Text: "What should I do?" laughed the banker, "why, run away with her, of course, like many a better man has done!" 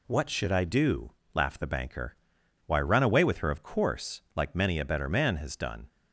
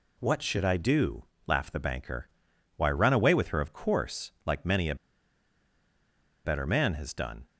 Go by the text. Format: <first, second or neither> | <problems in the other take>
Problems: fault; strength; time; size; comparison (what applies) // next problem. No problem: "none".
first | pauses between "a" and "better"; strong; at 4.9 s; 1.4 s long